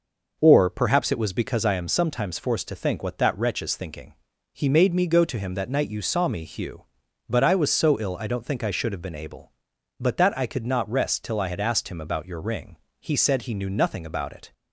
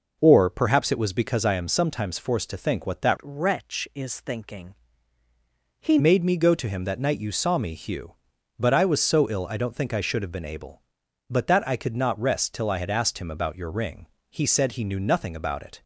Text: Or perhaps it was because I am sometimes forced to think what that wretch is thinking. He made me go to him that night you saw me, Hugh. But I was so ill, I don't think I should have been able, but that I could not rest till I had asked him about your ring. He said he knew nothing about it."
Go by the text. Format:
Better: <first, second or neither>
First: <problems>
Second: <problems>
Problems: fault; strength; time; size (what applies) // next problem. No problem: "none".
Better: first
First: none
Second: changes voice from "wretch" to "He"; from 3.2 to 5.9 s; 2.7 s long